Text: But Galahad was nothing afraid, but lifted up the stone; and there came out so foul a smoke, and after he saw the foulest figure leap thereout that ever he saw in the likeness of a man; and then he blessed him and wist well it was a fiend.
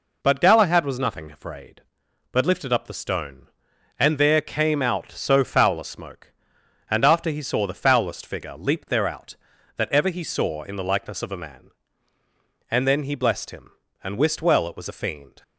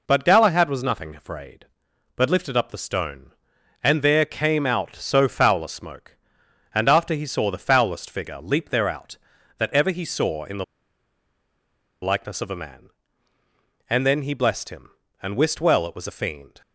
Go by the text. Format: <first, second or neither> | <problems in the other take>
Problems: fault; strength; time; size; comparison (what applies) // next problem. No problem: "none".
first | pauses between "the" and "likeness"; strong; at 10.6 s; 1.3 s long